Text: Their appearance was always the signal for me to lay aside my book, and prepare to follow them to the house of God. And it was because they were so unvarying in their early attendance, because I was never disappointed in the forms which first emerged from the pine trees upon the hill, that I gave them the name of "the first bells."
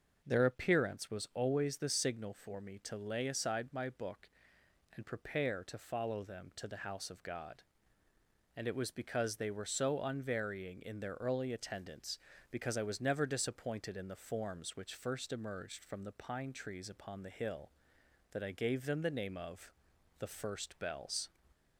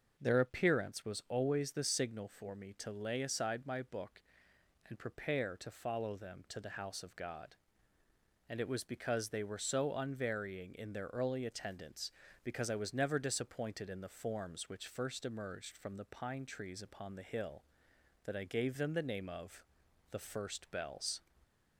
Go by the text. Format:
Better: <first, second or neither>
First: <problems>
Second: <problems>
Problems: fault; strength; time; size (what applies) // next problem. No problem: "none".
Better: neither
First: starts louder than the rest; noticeable; until 1.2 s; 6 dB // pauses between "of" and "the"; noticeable; at 19.7 s; 0.48 s long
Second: starts louder than the rest; until 1.1 s; 6 dB // pauses between "of" and "the"; noticeable; at 19.6 s; 0.48 s long